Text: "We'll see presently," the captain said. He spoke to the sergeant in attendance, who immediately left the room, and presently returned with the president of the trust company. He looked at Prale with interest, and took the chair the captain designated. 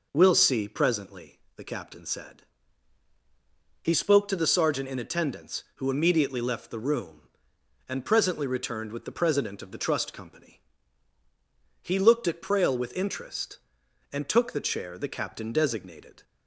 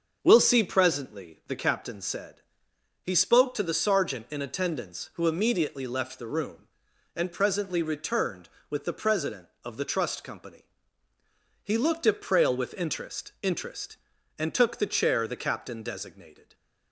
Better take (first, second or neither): first